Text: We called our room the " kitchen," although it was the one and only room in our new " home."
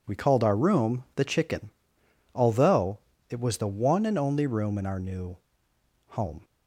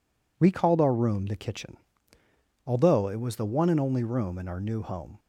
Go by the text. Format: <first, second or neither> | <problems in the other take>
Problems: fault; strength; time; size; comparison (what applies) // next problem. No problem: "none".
second | says "chicken" for "kitchen"; at 1.2 s // pauses between "although" and "it"; slight; at 2.9 s; 0.32 s long